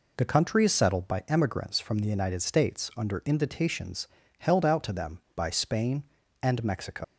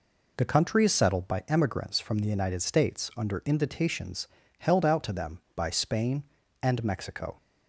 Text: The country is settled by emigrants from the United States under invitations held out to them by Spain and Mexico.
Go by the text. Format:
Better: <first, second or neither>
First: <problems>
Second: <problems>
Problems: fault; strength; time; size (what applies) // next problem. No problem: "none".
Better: second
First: pauses between "invitations" and "held"; slight; at 4.0 s; 0.32 s long // leaves "Mexico" unfinished; at 7.0 s; 125 ms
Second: pauses between "invitations" and "held"; slight; at 4.2 s; 0.32 s long